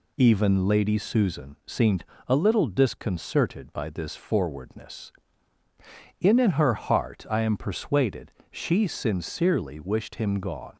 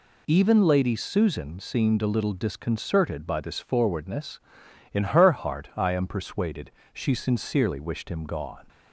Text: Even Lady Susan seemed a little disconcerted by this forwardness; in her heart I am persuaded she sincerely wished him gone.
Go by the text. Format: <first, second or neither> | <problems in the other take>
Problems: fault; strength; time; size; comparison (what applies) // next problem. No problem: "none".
second | pauses between "seemed" and "a"; slight; at 2.0 s; 0.24 s long // says "in" twice; at 6.3 s // pauses between "persuaded" and "she"; slight; at 8.2 s; 0.22 s long; slight in the second